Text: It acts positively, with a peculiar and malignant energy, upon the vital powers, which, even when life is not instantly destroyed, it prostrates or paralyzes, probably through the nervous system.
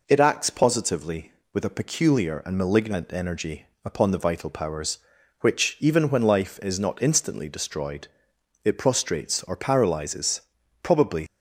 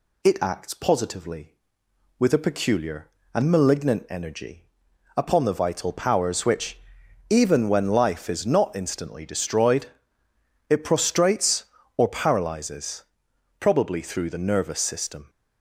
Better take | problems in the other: second | stops before "through the nervous system"; at 11.2 s

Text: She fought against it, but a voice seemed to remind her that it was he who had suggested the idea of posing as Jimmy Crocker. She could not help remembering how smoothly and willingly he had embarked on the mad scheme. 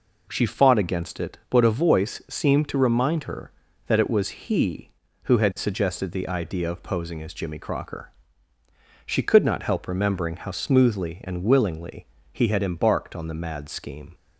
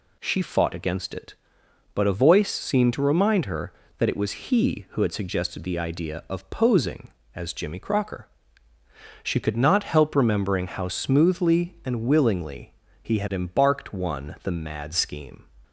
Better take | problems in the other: first | pauses between "willingly" and "he"; slight; at 12.7 s; 0.28 s long; slight in the first // says "one" for "on"; at 13.9 s

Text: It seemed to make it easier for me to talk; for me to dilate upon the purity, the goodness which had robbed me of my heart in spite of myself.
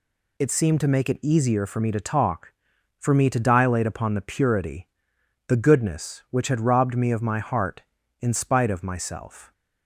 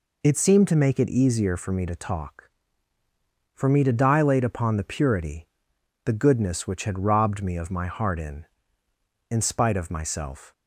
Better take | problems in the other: first | says "in" twice; at 9.3 s

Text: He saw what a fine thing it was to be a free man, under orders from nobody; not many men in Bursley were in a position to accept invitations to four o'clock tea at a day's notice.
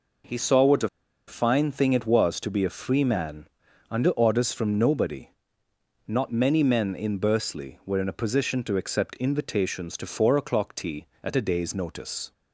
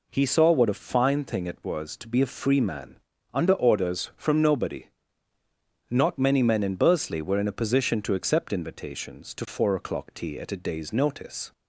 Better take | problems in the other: second | pauses between "a" and "fine"; at 0.8 s; 0.40 s long

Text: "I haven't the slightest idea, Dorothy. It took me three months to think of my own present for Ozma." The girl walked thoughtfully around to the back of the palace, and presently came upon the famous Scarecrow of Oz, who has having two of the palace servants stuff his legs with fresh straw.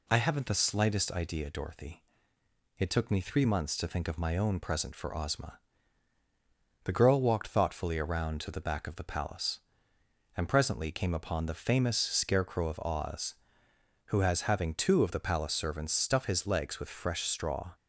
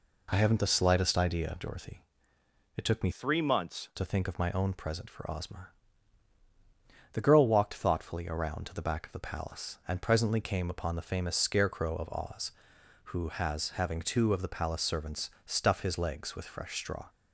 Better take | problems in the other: first | changes voice from "three" to "months"; from 3.1 to 3.8 s; 0.7 s long // pauses between "servants" and "stuff"; slight; at 15.2 s; 0.16 s long

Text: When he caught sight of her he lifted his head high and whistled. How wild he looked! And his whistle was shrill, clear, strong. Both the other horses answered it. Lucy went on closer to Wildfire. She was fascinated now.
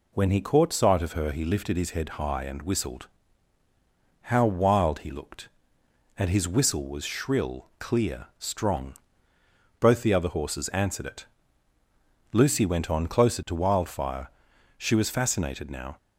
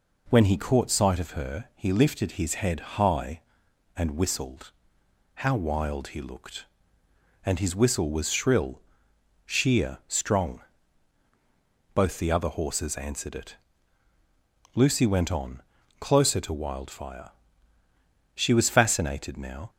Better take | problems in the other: first | pauses between "head" and "high"; slight; at 2.8 s; 0.18 s long // says "sheer" for "clear"; at 9.4 s // pauses between "on" and "closer"; at 15.6 s; 0.38 s long

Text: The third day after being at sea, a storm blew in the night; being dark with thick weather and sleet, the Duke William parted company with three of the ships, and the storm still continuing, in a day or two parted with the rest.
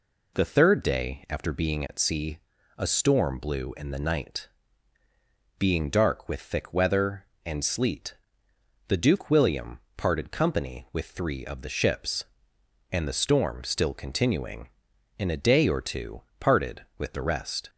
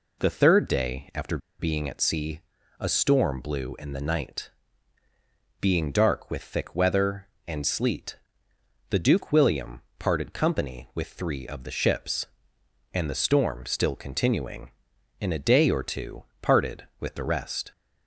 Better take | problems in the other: first | pauses between "after" and "being"; slight; at 1.3 s; 0.20 s long // pauses between "William" and "parted"; slight; at 9.8 s; 0.16 s long; slight in the first // pauses between "two" and "parted"; slight; at 16.2 s; 0.20 s long; slight in the first

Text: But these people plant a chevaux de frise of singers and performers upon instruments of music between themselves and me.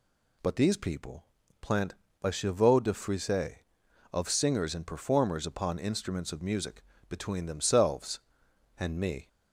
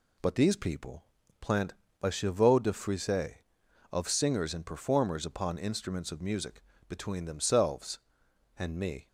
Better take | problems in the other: first | gets quieter; slight; throughout; 3 dB // pauses between "people" and "plant"; slight; at 1.0 s; 0.36 s long; slight in the first // pauses between "plant" and "a"; slight; at 1.7 s; 0.28 s long; slight in the first // pauses between "music" and "between"; slight; at 6.6 s; 0.28 s long; slight in the first

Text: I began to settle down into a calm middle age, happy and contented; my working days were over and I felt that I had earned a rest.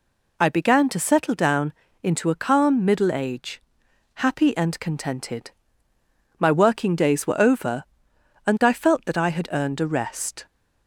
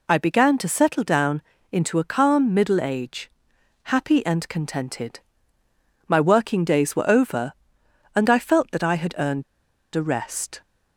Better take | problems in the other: first | pauses between "down" and "into"; slight; at 1.4 s; 0.28 s long; slight in the first // pauses between "earned" and "a"; noticeable; at 9.4 s; 0.52 s long

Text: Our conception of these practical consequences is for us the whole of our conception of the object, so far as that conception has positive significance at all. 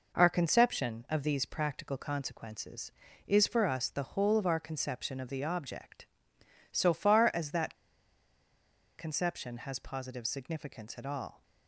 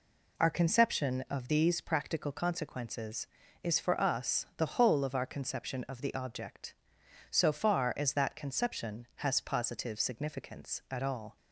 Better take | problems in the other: second | pauses between "that" and "conception"; strong; at 7.7 s; 1.2 s long

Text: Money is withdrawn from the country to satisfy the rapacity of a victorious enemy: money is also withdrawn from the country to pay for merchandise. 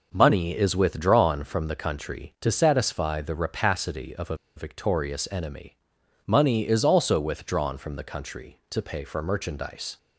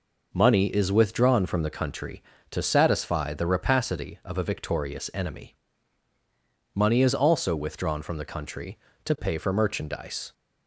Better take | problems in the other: second | pauses between "a" and "victorious"; slight; at 4.3 s; 0.20 s long

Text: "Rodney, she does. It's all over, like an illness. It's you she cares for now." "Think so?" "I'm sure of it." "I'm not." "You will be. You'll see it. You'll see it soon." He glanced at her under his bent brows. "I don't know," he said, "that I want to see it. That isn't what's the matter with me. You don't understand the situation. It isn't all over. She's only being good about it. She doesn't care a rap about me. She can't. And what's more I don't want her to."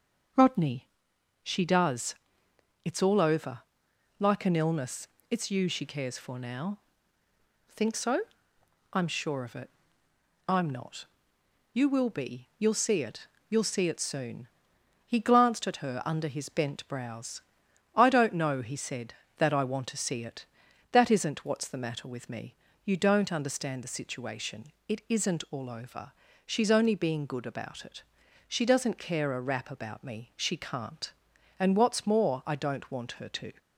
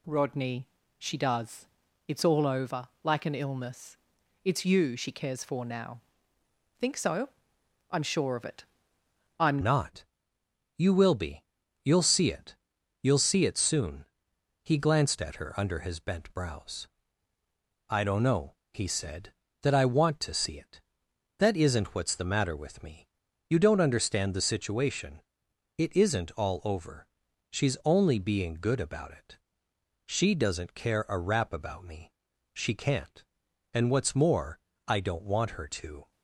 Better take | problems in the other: first | changes voice at "not"; from 9.6 s on; 26.5 s long // pauses between "more" and "I"; slight; at 34.5 s; 0.28 s long

